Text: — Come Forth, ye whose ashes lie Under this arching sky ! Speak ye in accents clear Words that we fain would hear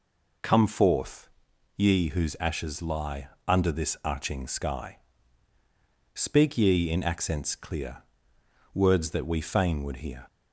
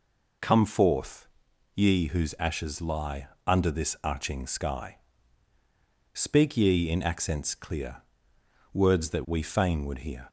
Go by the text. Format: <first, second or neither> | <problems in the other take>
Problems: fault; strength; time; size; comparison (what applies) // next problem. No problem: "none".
neither | pauses between "lie" and "Under"; slight; the same in both // pauses between "clear" and "Words"; noticeable; the same in both